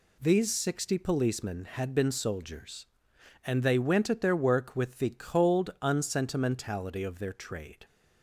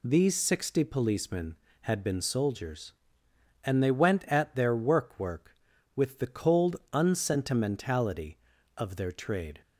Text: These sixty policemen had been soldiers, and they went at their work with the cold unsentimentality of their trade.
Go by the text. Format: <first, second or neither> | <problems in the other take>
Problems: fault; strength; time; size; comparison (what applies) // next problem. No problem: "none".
first | says "work" twice; at 5.1 s